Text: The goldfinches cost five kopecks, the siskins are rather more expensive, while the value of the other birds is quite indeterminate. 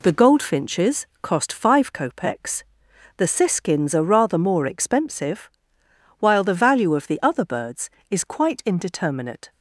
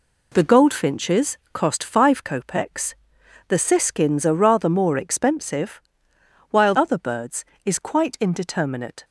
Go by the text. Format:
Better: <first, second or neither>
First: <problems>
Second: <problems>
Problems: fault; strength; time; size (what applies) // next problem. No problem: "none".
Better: first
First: pauses between "goldfinches" and "cost"; slight; at 1.0 s; 0.16 s long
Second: pauses between "goldfinches" and "cost"; slight; at 1.3 s; 0.16 s long // skips "the value of the"; at 6.7 s